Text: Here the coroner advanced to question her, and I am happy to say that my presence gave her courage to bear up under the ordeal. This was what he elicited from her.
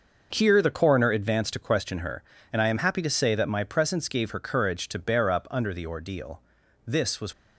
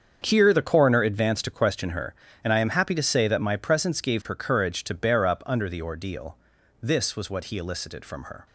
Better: second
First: starts louder than the rest; noticeable; until 1.3 s; 6 dB // stops before "what he elicited from her"; at 7.3 s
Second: starts louder than the rest; strong; until 1.2 s; 7 dB

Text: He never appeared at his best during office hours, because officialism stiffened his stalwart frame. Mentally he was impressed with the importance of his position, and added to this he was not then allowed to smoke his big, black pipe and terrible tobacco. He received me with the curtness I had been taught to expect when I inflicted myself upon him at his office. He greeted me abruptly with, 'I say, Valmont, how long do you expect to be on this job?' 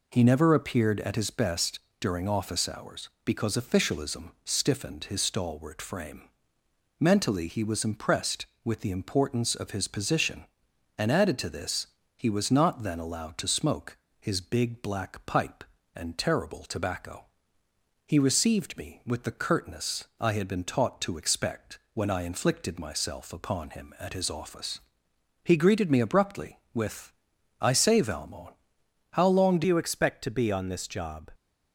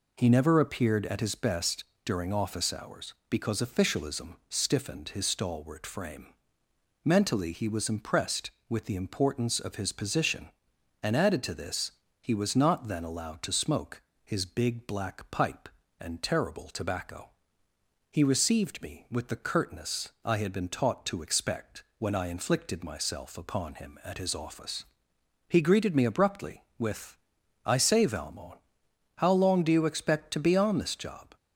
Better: second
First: pauses between "best" and "during"; slight; at 1.7 s; 0.20 s long // pauses between "this" and "he"; slight; at 11.8 s; 0.28 s long // pauses between "smoke" and "his"; slight; at 13.9 s; 0.22 s long // changes voice at "you"; from 29.6 s on; 1.7 s long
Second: pauses between "best" and "during"; slight; at 1.8 s; 0.20 s long // pauses between "this" and "he"; slight; at 11.9 s; 0.28 s long // pauses between "smoke" and "his"; slight; at 14.0 s; 0.22 s long

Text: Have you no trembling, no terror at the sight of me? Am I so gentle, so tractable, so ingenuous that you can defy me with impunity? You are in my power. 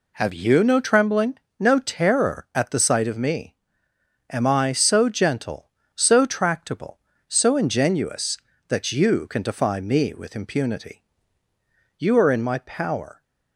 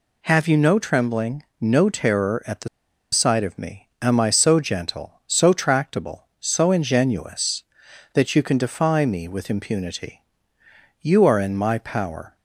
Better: first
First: none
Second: pauses between "the" and "sight"; at 2.6 s; 0.45 s long

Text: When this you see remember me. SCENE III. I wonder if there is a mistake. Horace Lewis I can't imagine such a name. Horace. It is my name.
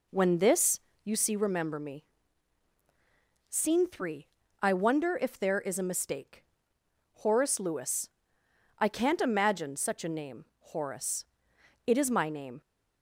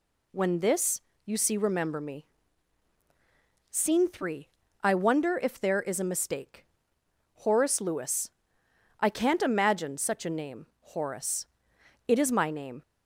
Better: second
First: starts louder than the rest; until 1.3 s; 3.5 dB // pauses between "this" and "you"; slight; at 0.8 s; 0.24 s long // pauses between "Lewis" and "I"; noticeable; at 8.0 s; 0.70 s long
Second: pauses between "this" and "you"; slight; at 1.0 s; 0.24 s long // pauses between "Lewis" and "I"; noticeable; at 8.2 s; 0.70 s long

